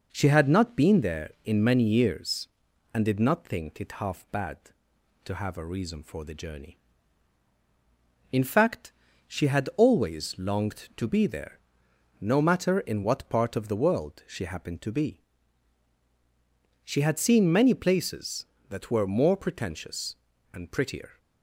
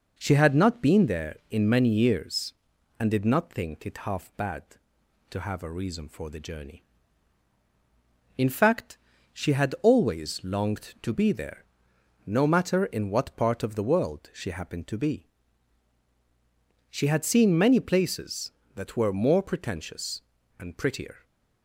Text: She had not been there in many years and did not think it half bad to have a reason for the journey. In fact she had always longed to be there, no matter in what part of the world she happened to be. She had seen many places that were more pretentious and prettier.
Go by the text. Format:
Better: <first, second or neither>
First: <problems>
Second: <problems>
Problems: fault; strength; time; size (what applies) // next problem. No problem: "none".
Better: neither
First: pauses between "fact" and "she"; at 8.9 s; 0.38 s long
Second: pauses between "fact" and "she"; at 8.9 s; 0.38 s long